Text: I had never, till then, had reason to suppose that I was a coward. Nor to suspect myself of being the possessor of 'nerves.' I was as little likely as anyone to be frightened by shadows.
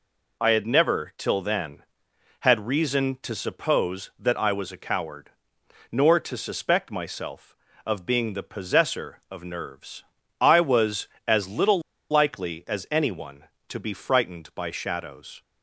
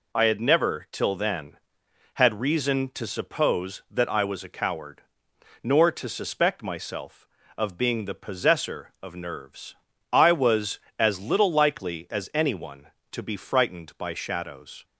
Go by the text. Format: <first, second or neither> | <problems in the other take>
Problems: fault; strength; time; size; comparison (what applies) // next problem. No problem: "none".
second | pauses between "little" and "likely"; slight; at 11.8 s; 0.30 s long